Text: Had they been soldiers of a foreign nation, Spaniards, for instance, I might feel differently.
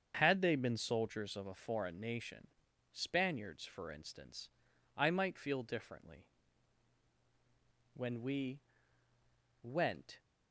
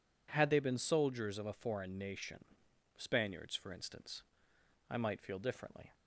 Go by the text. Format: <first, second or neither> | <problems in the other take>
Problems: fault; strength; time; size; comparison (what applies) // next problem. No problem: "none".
second | starts louder than the rest; until 1.2 s; 7 dB // goes on to say "When we went"; strong; from 7.9 s on; 2.2 s long